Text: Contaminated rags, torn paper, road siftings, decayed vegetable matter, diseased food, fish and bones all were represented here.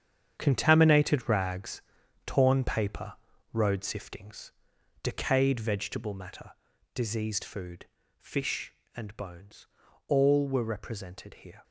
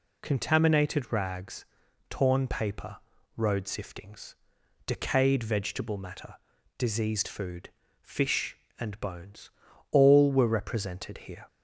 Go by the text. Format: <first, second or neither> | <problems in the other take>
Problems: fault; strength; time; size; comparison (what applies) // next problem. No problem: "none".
second | gets quieter; strong; throughout; 11.5 dB // pauses between "bones" and "all"; at 9.6 s; 0.42 s long; also in the second